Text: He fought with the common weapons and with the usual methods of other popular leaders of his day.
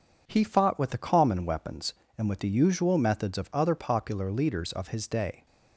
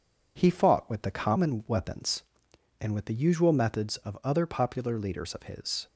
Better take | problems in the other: first | stops before "day"; at 5.8 s

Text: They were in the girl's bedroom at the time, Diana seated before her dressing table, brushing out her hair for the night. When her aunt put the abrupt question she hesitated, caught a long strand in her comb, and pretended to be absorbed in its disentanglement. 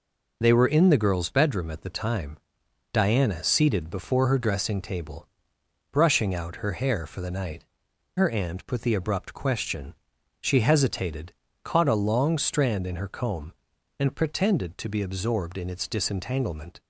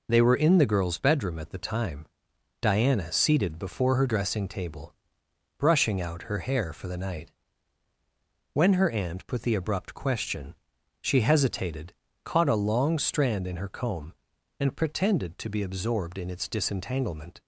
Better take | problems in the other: second | skips "When"; at 7.9 s // pauses between "question" and "she"; noticeable; at 9.9 s; 0.48 s long; noticeable in the second

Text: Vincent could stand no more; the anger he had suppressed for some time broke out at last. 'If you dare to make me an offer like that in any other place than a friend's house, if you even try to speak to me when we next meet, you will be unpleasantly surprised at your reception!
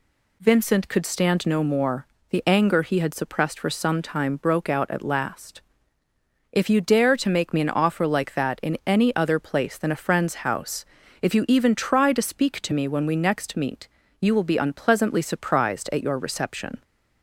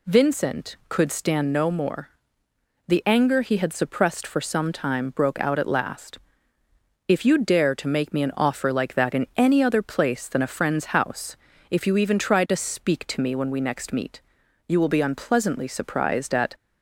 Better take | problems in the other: first | stops before "your reception"; at 16.5 s

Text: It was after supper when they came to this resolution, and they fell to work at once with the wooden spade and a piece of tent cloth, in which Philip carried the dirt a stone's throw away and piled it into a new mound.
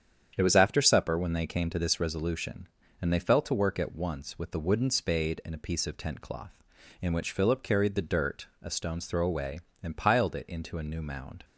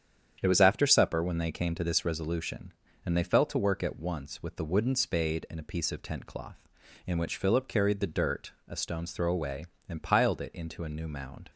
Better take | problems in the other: neither | starts louder than the rest; strong; the same in both // pauses between "dirt" and "a"; slight; the same in both

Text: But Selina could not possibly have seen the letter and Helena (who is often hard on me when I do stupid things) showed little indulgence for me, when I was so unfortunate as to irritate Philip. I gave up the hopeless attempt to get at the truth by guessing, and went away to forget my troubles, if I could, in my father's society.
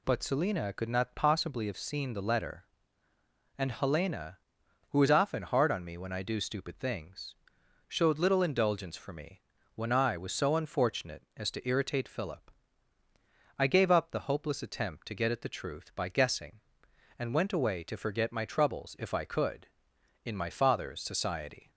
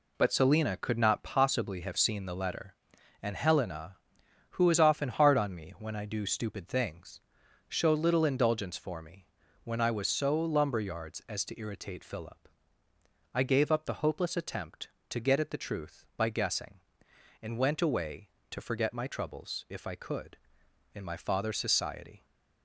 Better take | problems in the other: first | says "lumberyards" for "unfortunate"; at 10.3 s

